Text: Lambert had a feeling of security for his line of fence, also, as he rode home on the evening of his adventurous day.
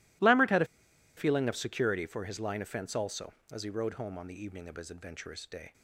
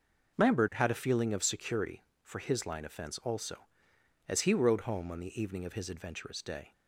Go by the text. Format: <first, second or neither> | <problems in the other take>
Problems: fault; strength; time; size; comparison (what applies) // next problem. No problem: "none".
second | pauses between "a" and "feeling"; noticeable; at 0.6 s; 0.51 s long